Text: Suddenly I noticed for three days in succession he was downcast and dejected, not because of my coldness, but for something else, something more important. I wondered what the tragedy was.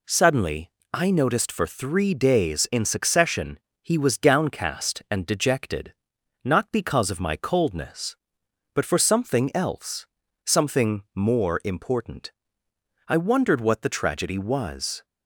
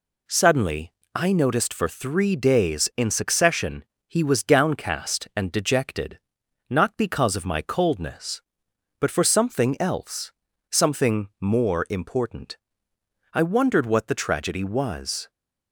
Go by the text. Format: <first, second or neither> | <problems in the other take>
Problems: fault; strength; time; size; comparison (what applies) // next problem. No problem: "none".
neither | pauses between "Suddenly" and "I"; slight; the same in both // pauses between "succession" and "he"; slight; the same in both